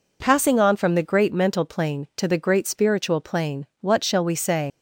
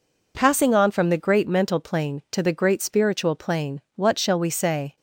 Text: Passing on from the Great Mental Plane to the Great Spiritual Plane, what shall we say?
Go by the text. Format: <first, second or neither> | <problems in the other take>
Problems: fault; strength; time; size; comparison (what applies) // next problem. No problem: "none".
second | leaves "say" unfinished; at 4.7 s; 110 ms